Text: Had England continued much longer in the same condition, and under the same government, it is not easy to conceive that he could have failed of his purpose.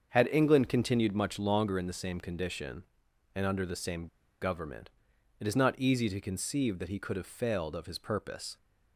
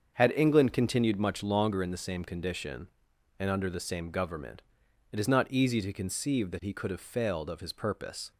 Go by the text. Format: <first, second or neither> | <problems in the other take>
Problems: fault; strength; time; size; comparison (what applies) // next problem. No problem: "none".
second | starts louder than the rest; until 1.1 s; 7 dB; also in the second // pauses between "same" and "government"; slight; at 4.0 s; 0.34 s long